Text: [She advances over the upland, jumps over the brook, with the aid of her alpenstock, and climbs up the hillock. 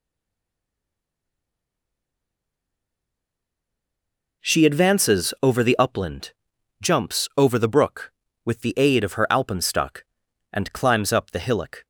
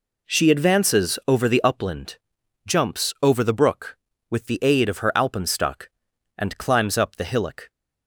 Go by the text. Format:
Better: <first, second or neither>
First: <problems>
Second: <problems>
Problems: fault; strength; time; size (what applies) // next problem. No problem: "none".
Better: second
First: stays silent before the first word; strong; until 4.4 s; 4.4 s long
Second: none